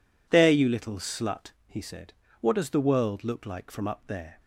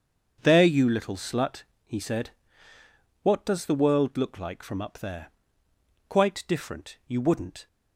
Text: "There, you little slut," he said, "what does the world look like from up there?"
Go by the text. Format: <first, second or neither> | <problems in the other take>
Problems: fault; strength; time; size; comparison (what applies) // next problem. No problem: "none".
first | starts louder than the rest; until 1.4 s; 7 dB // goes on to say "Quite different you wouldn't"; from 6.0 s on; 1.6 s long